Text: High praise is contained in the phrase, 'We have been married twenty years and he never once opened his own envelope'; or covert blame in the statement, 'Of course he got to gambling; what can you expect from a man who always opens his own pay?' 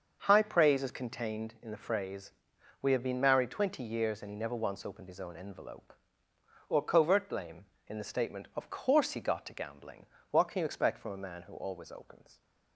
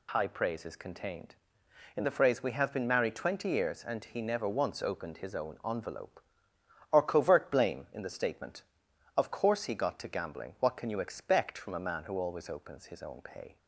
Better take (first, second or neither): second